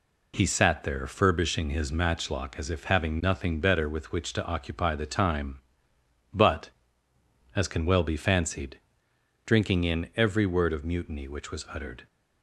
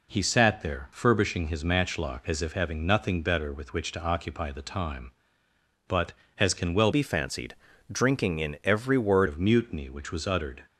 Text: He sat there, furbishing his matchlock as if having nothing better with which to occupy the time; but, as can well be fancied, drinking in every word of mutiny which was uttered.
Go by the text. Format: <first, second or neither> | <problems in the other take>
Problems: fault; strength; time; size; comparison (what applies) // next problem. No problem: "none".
first | changes voice from "be" to "word"; from 6.9 to 9.2 s; 2.3 s long